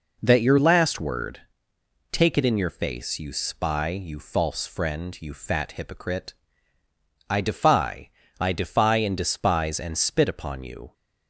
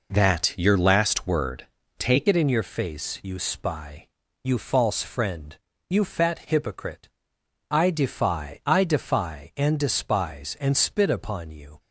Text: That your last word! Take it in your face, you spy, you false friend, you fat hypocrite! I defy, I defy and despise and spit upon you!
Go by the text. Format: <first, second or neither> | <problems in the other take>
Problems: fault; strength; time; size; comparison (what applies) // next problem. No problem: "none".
first | changes voice at "it"; from 2.2 s on; 9.5 s long